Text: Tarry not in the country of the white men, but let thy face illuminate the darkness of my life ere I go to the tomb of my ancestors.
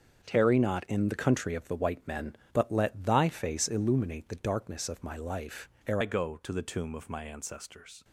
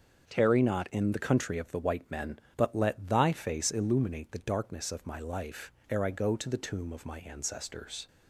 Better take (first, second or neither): second